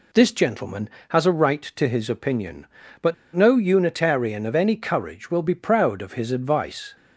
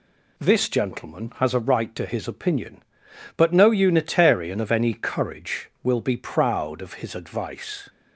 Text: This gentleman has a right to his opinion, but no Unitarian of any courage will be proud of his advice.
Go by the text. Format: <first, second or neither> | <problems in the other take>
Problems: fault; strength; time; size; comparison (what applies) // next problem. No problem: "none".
second | pauses between "but" and "no"; slight; at 3.1 s; 0.21 s long